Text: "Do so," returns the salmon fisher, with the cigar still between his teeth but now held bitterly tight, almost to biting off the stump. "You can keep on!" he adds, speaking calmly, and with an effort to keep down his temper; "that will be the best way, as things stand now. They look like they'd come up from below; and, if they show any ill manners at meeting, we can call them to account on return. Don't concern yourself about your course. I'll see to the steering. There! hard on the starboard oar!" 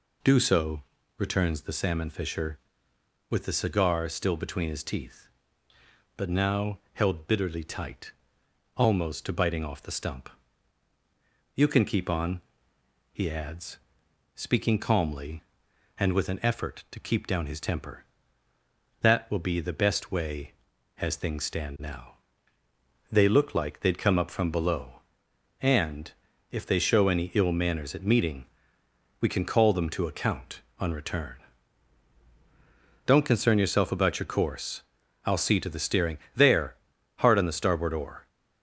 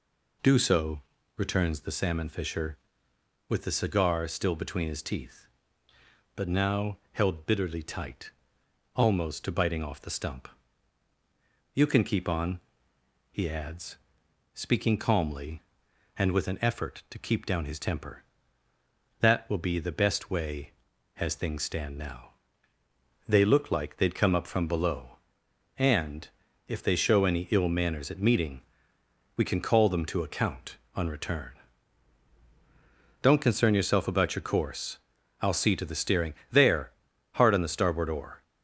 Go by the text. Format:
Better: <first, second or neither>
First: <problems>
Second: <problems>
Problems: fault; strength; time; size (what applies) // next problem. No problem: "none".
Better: neither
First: none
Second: none